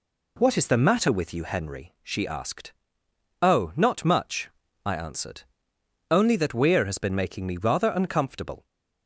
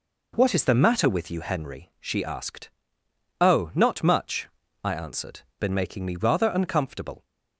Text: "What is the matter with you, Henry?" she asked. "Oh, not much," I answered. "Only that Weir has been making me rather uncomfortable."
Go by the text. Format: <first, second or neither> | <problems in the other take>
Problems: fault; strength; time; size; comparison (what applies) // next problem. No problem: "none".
first | skips "Only that Weir has"; at 5.5 s